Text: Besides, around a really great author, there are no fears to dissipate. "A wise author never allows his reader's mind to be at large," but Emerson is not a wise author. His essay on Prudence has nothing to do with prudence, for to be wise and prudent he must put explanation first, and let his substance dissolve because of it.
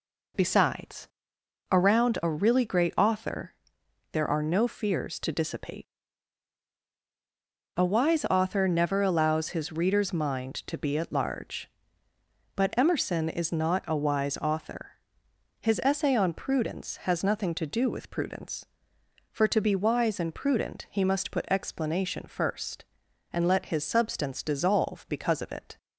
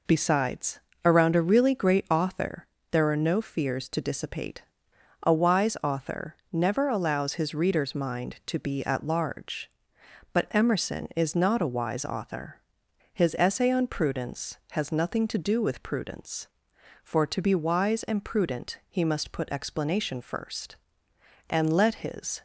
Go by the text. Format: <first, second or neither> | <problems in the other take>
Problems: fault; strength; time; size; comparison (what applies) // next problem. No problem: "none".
first | pauses between "author" and "never"; slight; at 6.3 s; 0.16 s long // stops before "substance dissolve because of it"; at 22.3 s